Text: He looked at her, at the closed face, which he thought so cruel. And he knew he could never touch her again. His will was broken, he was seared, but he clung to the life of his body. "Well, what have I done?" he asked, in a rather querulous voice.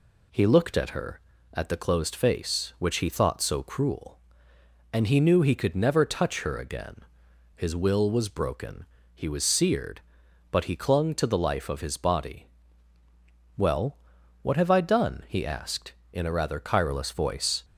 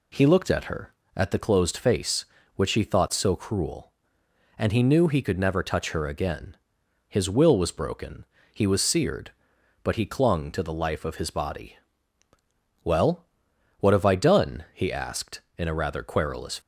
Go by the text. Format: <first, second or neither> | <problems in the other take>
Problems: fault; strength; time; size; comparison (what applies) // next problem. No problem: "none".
first | stops before "voice"; at 16.5 s